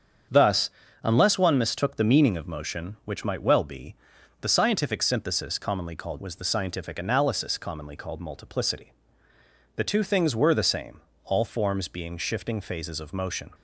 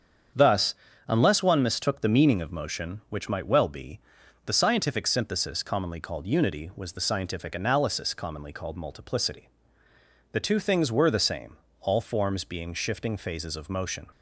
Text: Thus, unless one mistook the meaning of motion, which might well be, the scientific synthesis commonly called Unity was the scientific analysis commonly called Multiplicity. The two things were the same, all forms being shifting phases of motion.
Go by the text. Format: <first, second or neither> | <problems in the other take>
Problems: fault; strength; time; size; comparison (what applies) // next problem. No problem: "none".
second | starts louder than the rest; strong; until 1.6 s; 7.5 dB; strong in the second // skips "Unity"; at 6.1 s